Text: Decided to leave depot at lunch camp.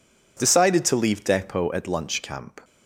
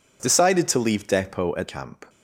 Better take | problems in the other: first | skips "lunch"; at 1.6 s

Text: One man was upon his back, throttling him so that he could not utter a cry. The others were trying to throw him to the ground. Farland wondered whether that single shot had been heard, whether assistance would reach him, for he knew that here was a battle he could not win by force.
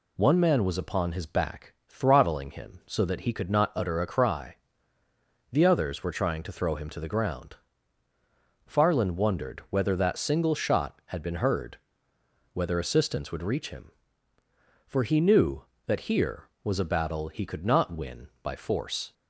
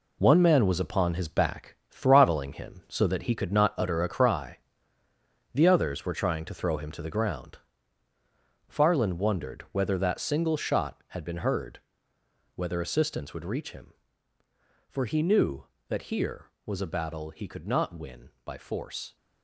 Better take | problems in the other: first | gets quieter; strong; throughout; 9 dB

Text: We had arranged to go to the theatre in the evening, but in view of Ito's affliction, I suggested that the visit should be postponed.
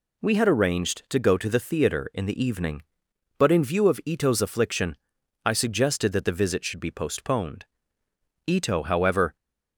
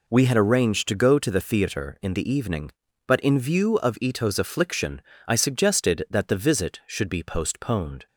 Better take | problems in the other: second | goes on to say "Ito however"; noticeable; from 8.4 s on; 0.88 s long

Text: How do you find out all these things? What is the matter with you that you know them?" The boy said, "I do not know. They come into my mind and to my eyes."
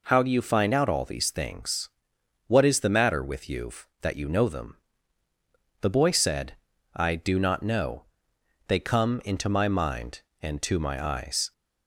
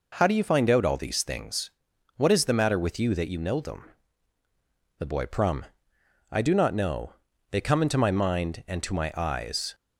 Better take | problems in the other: first | says "prum" for "said"; at 5.2 s

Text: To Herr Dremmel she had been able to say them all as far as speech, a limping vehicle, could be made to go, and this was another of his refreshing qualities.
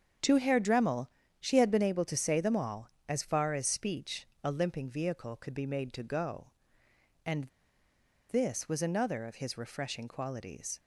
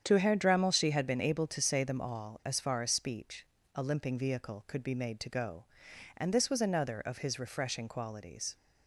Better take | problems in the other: second | starts louder than the rest; strong; until 1.5 s; 7 dB; strong in the second // pauses between "Dremmel" and "she"; slight; at 1.0 s; 0.32 s long // pauses between "and" and "this"; noticeable; at 7.4 s; 0.85 s long

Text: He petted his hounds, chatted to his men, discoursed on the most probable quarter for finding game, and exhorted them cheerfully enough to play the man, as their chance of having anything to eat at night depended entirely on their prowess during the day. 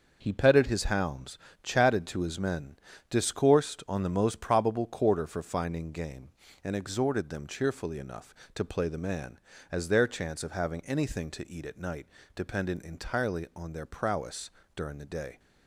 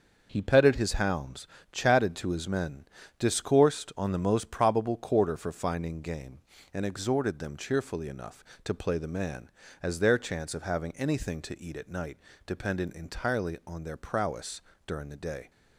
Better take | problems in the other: neither | starts louder than the rest; the same in both // pauses between "night" and "depended"; slight; the same in both // pauses between "prowess" and "during"; slight; the same in both

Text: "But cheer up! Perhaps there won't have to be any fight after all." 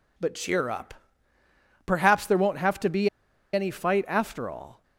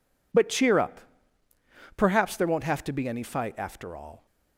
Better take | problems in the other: second | pauses between "be" and "any"; at 3.0 s; 0.45 s long

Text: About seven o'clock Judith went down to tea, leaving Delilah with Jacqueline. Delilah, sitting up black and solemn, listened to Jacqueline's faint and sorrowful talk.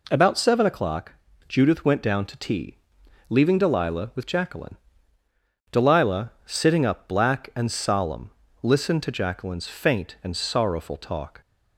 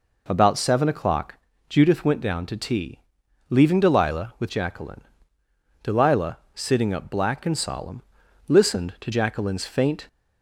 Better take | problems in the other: first | pauses between "o'clock" and "Judith"; slight; at 1.3 s; 0.34 s long; slight in the first // stops before "and sorrowful talk"; at 10.0 s

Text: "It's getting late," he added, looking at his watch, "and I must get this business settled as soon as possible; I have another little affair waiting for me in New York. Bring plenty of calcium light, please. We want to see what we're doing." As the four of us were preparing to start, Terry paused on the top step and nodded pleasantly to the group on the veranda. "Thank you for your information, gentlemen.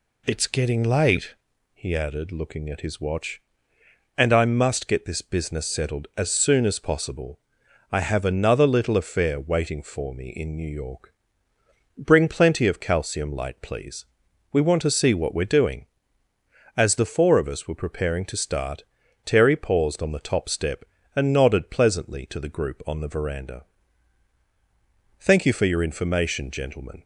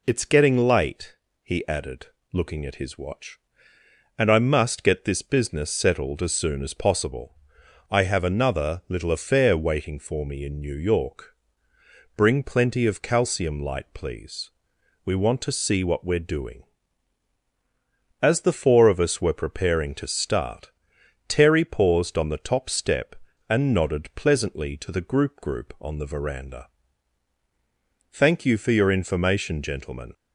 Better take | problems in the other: first | says "group" twice; at 25.3 s

